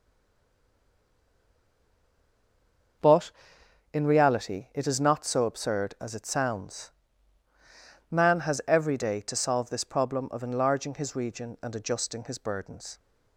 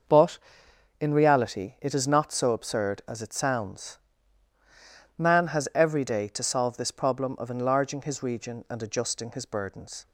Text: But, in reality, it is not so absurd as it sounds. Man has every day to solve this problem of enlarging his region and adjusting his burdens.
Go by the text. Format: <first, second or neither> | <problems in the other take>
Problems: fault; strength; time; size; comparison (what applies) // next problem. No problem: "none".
second | stays silent before the first word; strong; until 3.0 s; 3.0 s long // starts louder than the rest; until 4.6 s; 6 dB; also in the second